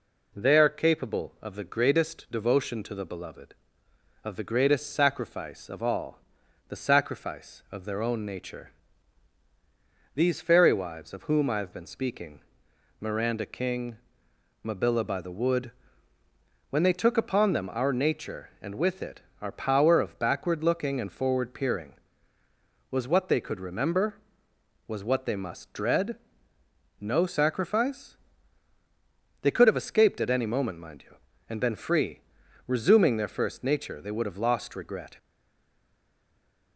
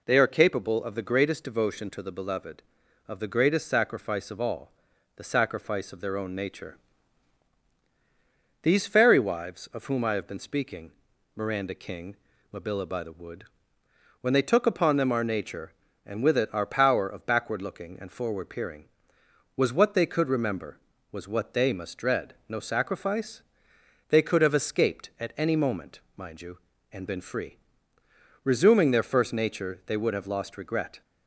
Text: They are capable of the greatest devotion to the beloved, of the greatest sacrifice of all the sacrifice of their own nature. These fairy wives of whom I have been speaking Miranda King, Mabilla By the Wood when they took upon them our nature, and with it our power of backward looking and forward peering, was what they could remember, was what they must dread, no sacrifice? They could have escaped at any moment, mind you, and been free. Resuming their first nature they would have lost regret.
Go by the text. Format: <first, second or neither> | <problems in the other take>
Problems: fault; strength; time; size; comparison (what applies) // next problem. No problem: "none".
second | pauses between "all" and "the"; noticeable; at 6.1 s; 0.50 s long; also in the second // pauses between "speaking" and "Miranda"; noticeable; at 12.3 s; 0.60 s long; also in the second // pauses between "Wood" and "when"; at 15.7 s; 1.0 s long; noticeable in the second // pauses between "it" and "our"; slight; at 19.2 s; 0.22 s long // stays silent after the last word; noticeable; from 35.1 s on; 1.6 s long